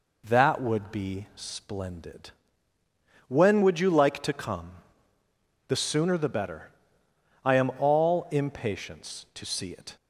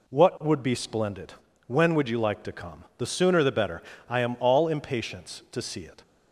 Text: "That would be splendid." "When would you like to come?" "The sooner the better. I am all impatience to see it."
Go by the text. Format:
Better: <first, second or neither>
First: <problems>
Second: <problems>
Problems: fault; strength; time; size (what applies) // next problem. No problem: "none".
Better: first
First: none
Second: says "What" for "That"; at 0.0 s